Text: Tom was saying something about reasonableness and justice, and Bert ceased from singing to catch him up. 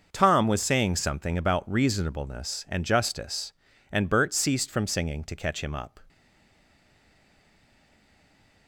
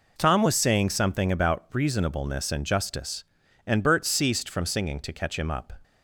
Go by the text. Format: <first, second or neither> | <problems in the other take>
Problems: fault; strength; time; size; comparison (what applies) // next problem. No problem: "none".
second | starts louder than the rest; until 1.1 s; 6 dB // stays silent after the last word; strong; from 6.0 s on; 2.6 s long